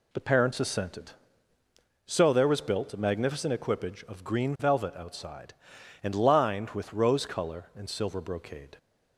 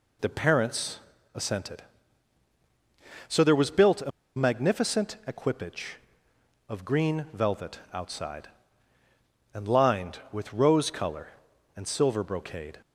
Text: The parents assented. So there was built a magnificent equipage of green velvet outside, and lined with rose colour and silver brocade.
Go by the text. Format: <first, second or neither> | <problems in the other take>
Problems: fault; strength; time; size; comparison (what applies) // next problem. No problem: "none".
first | pauses between "parents" and "assented"; slight; at 1.0 s; 0.34 s long // pauses between "a" and "magnificent"; slight; at 4.1 s; 0.25 s long